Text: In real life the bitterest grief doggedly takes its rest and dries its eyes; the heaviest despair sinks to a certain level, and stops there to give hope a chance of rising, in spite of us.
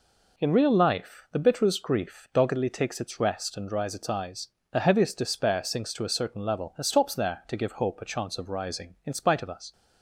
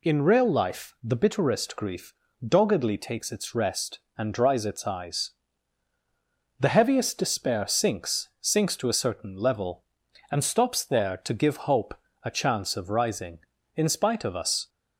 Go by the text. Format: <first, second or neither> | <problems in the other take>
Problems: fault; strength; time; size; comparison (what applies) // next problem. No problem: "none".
first | pauses between "grief" and "doggedly"; slight; at 2.1 s; 0.32 s long // says "sinks" twice; at 8.4 s // pauses between "hope" and "a"; slight; at 11.9 s; 0.30 s long